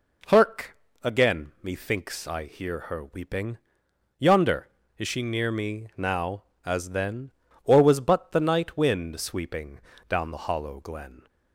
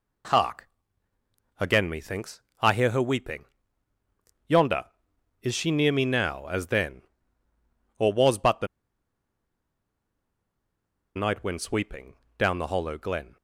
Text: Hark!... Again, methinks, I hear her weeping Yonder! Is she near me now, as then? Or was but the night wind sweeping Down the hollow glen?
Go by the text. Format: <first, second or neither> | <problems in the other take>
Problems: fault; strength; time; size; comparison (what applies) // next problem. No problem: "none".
first | pauses between "weeping" and "Yonder"; at 3.4 s; 1.0 s long; noticeable in the first // pauses between "the" and "night"; strong; at 8.6 s; 2.4 s long // pauses between "sweeping" and "Down"; slight; at 12.1 s; 0.22 s long; slight in the first